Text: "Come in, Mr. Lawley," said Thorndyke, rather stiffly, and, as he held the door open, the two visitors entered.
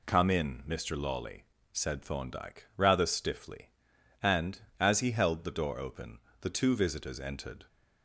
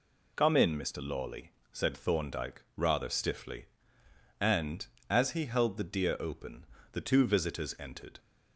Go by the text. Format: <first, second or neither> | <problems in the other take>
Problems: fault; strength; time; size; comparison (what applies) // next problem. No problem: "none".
first | says "deer" for "door"; at 5.8 s